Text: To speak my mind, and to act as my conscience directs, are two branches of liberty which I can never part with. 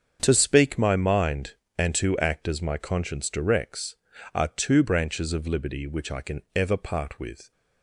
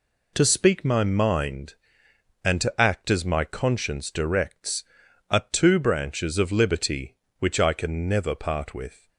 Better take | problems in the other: second | starts louder than the rest; strong; until 1.2 s; 7.5 dB // says "ever" for "never"; at 6.5 s

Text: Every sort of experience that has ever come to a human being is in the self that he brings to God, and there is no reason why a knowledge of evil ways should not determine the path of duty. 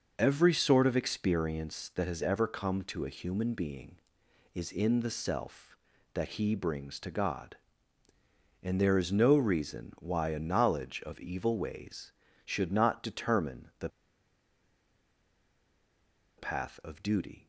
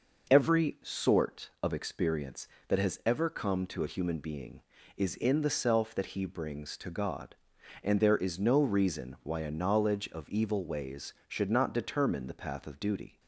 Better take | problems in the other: second | pauses between "the" and "path"; strong; at 13.8 s; 2.4 s long

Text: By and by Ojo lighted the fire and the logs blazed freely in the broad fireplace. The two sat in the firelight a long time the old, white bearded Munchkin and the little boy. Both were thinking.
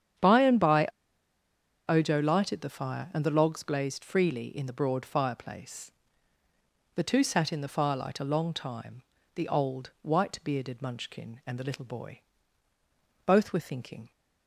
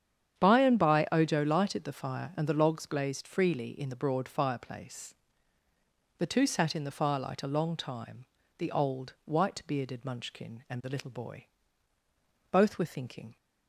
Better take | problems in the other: second | starts louder than the rest; strong; until 2.2 s; 8.5 dB; strong in the second // pauses between "by" and "Ojo"; at 0.8 s; 1.0 s long // pauses between "time" and "the"; slight; at 9.0 s; 0.32 s long; slight in the second

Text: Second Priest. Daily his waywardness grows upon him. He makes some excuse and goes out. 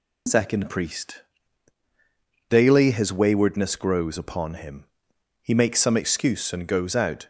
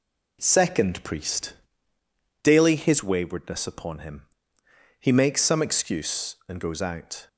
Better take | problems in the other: first | skips "grows"; at 3.6 s

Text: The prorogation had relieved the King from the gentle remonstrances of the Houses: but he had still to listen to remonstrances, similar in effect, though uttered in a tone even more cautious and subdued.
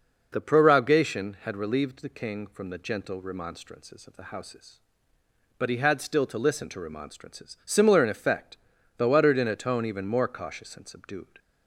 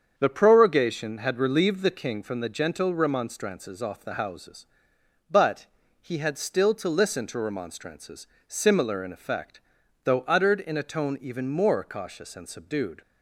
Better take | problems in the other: first | starts louder than the rest; strong; until 1.2 s; 7 dB // says "off" for "of"; at 3.8 s // pauses between "but" and "he"; slight; at 5.6 s; 0.34 s long

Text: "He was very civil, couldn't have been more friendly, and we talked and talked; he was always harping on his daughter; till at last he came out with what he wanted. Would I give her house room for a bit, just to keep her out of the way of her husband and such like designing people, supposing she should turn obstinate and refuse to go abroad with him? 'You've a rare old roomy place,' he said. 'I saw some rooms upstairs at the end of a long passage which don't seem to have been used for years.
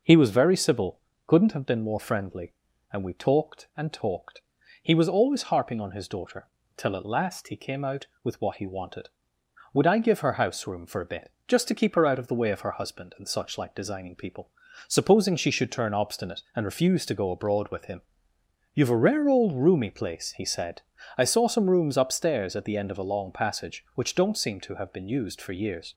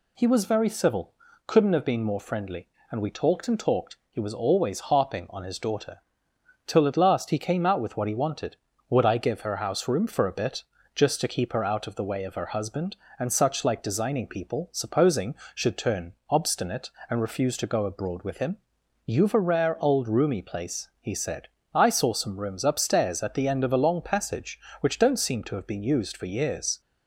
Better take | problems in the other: first | skips "she"; at 15.4 s // pauses between "turn" and "obstinate"; slight; at 16.1 s; 0.16 s long

